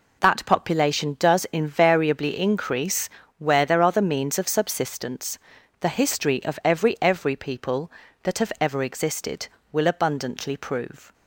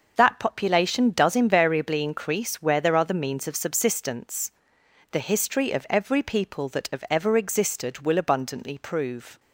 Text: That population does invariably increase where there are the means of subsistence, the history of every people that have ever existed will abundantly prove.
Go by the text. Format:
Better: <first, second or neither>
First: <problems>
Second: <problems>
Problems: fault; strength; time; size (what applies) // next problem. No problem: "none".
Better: second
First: pauses between "increase" and "where"; slight; at 3.0 s; 0.28 s long // says "every" twice; at 7.0 s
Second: none